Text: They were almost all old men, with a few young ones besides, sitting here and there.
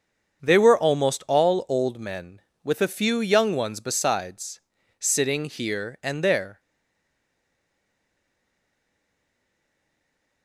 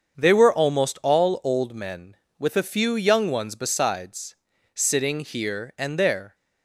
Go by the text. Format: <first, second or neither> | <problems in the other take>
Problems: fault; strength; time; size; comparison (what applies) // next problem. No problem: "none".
second | starts louder than the rest; until 1.4 s; 7 dB; also in the second // stays silent after the last word; strong; from 6.5 s on; 3.9 s long